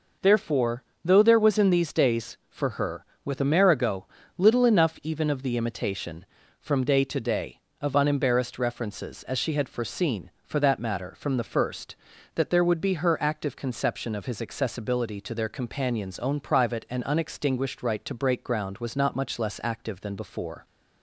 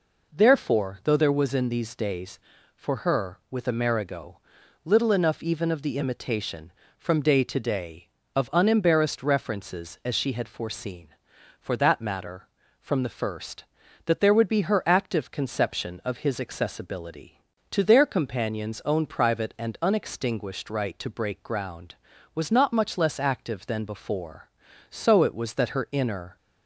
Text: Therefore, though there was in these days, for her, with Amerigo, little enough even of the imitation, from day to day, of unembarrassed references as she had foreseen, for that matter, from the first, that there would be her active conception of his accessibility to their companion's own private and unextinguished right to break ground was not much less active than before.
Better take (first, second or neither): first